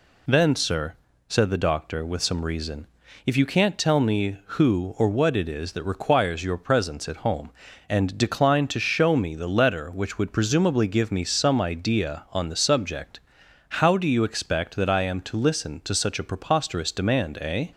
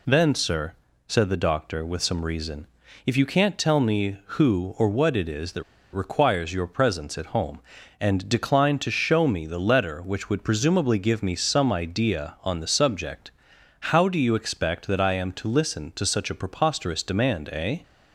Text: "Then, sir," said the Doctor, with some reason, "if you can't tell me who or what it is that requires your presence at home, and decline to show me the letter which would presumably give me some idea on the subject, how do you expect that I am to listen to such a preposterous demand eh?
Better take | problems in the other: first | pauses between "that" and "requires"; slight; at 5.6 s; 0.29 s long

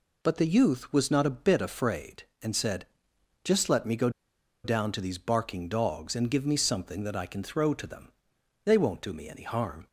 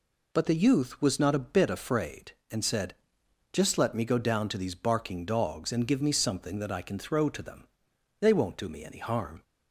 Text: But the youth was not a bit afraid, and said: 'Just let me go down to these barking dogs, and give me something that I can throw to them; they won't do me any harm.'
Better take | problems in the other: second | pauses between "go" and "down"; noticeable; at 4.0 s; 0.55 s long

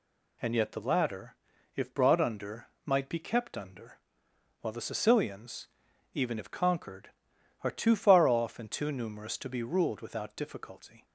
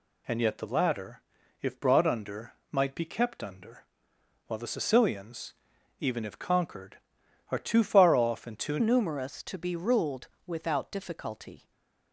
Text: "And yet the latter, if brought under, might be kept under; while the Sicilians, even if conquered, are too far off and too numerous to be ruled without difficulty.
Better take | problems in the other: first | changes voice at "numerous"; from 8.7 s on; 3.0 s long // pauses between "ruled" and "without"; slight; at 10.2 s; 0.18 s long // stays silent after the last word; slight; from 11.5 s on; 0.6 s long

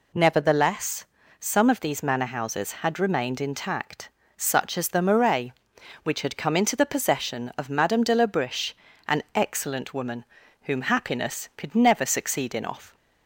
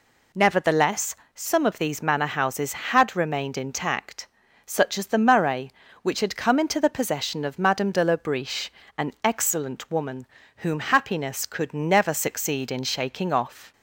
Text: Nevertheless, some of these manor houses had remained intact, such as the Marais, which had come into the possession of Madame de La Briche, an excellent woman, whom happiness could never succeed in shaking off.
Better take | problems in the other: second | skips "shaking"; at 12.6 s

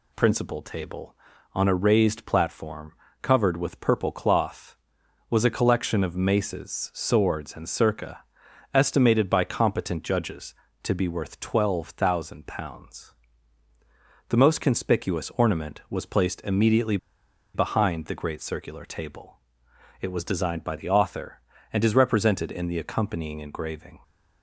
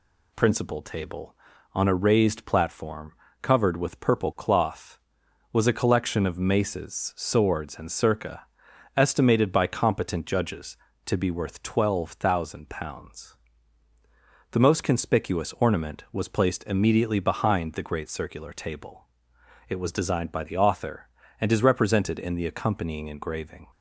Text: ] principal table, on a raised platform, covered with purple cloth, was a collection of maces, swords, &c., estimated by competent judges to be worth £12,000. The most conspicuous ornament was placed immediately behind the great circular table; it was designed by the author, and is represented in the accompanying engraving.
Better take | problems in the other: second | pauses between "immediately" and "behind"; noticeable; at 16.9 s; 0.57 s long

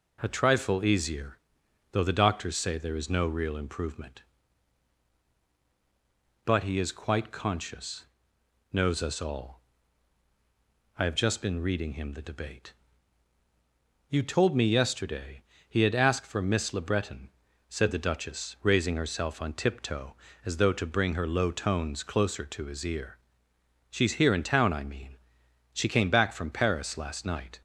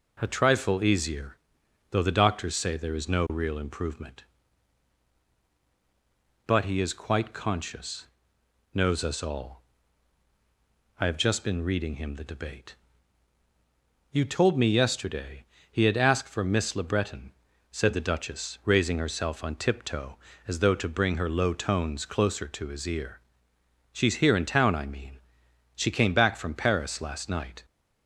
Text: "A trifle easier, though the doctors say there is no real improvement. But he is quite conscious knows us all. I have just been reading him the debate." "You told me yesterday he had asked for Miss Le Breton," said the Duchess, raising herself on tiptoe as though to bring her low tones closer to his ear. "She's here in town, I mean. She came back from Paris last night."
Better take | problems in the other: neither | pauses between "conscious" and "knows"; noticeable; the same in both // pauses between "yesterday" and "he"; slight; the same in both

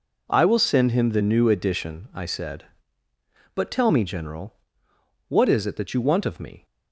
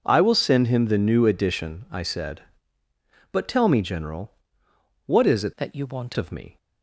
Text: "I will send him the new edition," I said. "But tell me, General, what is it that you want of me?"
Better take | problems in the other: first | changes voice from "that" to "want"; from 5.5 to 6.1 s; 0.6 s long

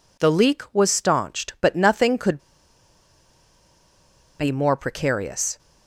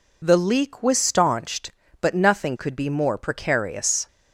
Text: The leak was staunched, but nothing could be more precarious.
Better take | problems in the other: second | pauses between "could" and "be"; strong; at 2.3 s; 2.0 s long

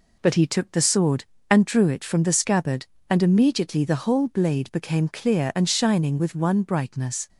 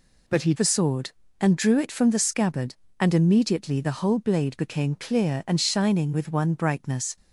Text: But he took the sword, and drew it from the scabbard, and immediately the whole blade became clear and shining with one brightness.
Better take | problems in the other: first | skips "took"; at 0.5 s

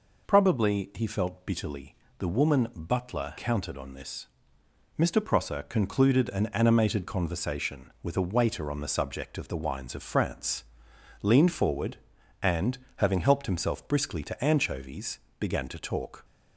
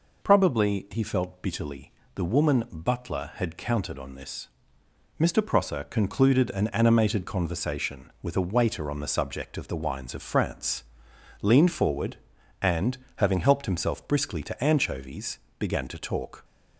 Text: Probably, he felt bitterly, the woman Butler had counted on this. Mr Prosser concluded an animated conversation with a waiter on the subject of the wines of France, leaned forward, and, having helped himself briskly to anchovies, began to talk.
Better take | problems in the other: second | skips "had"; at 3.3 s

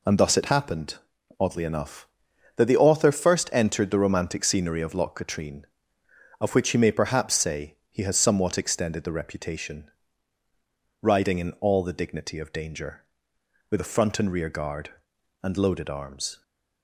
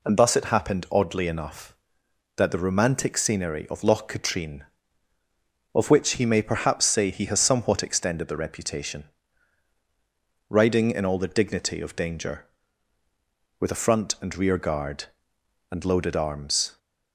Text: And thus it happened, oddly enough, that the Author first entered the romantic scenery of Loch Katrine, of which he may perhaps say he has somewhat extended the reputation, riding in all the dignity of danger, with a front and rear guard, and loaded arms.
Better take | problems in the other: first | skips "the Author first entered"; at 2.5 s

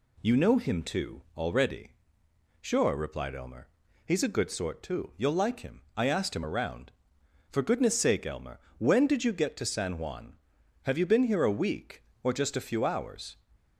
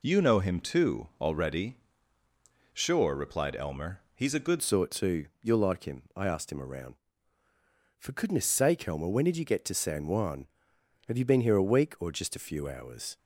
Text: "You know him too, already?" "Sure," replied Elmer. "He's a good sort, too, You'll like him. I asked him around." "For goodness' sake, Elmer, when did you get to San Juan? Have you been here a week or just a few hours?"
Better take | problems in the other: first | changes voice at "sort"; from 4.6 s on; 8.5 s long

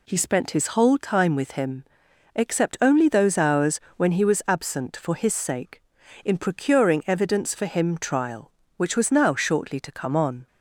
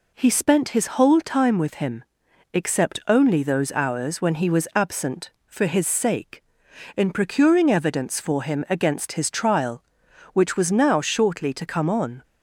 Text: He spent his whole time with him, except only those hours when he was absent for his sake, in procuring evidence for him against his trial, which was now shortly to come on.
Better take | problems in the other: second | pauses between "hours" and "when"; slight; at 3.8 s; 0.16 s long // skips "against his"; at 7.9 s

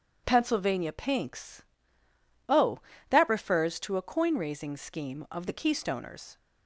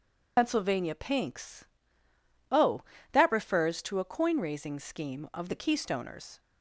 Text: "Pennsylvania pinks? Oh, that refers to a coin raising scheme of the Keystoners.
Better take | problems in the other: first | loses the start of "Pennsylvania"; at 0.3 s; 95 ms

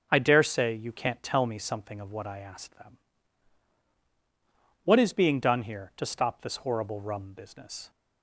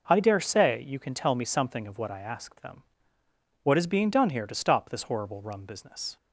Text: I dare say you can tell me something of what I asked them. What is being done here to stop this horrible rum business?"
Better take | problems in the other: second | starts louder than the rest; until 1.1 s; 6.5 dB // says "can't" for "can"; at 0.9 s

